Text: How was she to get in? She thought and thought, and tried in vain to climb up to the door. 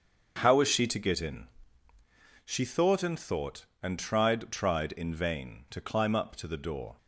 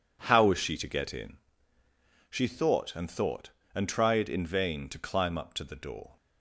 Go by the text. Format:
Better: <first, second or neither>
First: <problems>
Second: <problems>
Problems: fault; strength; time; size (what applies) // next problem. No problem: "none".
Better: second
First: starts louder than the rest; until 1.4 s; 6.5 dB // says "tried" twice; at 4.5 s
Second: none